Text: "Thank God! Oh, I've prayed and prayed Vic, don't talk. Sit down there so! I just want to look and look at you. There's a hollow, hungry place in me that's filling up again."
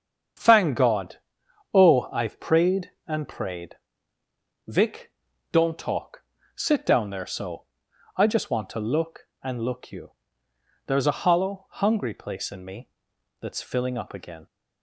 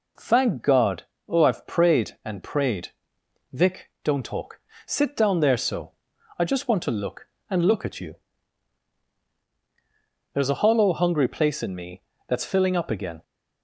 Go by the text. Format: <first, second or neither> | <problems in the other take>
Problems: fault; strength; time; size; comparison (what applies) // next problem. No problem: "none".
second | starts louder than the rest; strong; until 1.9 s; 7.5 dB // pauses between "prayed" and "Vic"; noticeable; at 3.7 s; 0.92 s long; noticeable in the second // skips "at"; at 9.8 s // pauses between "me" and "that's"; noticeable; at 12.8 s; 0.52 s long; slight in the second